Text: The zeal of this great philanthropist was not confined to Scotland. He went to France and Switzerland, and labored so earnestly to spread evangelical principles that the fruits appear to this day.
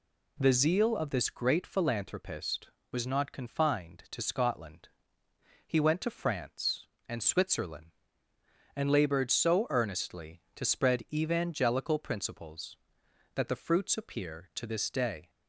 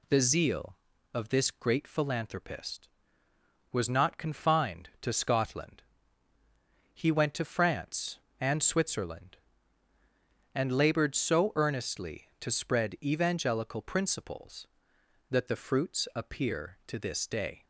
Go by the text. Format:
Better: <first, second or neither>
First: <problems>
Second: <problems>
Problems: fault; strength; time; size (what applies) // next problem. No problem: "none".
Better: neither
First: none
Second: none